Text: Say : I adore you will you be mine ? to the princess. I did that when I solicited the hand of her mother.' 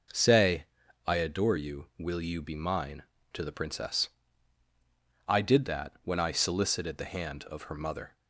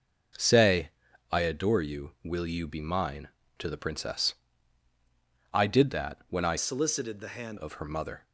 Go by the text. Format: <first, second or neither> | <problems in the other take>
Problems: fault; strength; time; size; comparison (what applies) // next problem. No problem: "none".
first | changes voice from "solicited" to "hand"; from 6.5 to 7.5 s; 1.0 s long